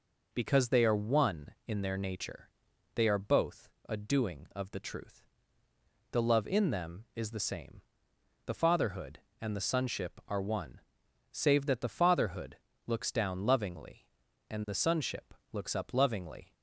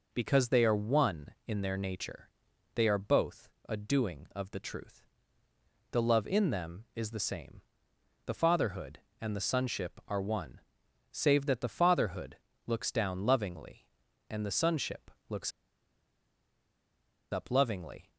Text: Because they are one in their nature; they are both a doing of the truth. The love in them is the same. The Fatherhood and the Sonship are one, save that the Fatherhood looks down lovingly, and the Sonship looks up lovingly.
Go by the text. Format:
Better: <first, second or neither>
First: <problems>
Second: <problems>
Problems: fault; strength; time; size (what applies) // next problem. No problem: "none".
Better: first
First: pauses between "both" and "a"; slight; at 3.6 s; 0.20 s long // pauses between "Fatherhood" and "looks"; slight; at 12.5 s; 0.28 s long // pauses between "Sonship" and "looks"; slight; at 15.3 s; 0.18 s long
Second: pauses between "both" and "a"; slight; at 3.4 s; 0.20 s long // pauses between "Fatherhood" and "looks"; slight; at 12.3 s; 0.28 s long // pauses between "Sonship" and "looks"; slight; at 15.1 s; 0.18 s long // pauses between "looks" and "up"; strong; at 15.5 s; 1.8 s long